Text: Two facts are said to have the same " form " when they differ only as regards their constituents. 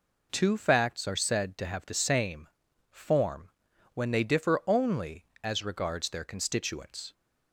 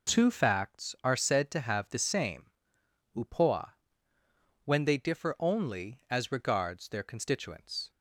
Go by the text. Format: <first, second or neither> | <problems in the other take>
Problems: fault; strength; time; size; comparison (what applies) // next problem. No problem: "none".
first | says "upoa" for "form"; at 3.1 s